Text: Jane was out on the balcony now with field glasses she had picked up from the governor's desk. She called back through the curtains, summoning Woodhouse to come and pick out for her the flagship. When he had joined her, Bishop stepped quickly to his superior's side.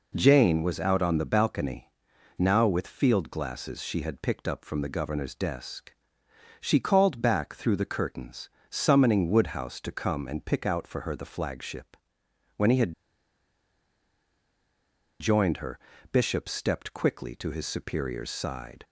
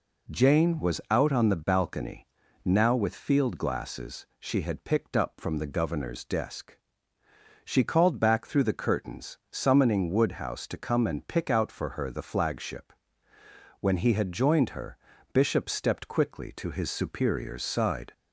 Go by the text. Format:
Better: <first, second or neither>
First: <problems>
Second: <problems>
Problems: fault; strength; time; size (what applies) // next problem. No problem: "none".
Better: second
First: pauses between "balcony" and "now"; noticeable; at 1.8 s; 0.48 s long // pauses between "had" and "joined"; strong; at 12.9 s; 2.2 s long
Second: pauses between "balcony" and "now"; slight; at 2.2 s; 0.36 s long